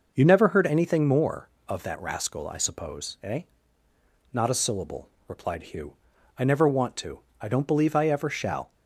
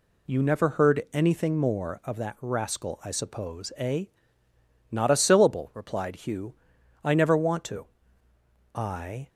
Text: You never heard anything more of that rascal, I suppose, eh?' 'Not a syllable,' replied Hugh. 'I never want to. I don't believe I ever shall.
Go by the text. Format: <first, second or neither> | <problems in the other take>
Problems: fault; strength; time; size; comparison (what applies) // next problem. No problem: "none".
first | stops before "don't believe I ever shall"; at 9.2 s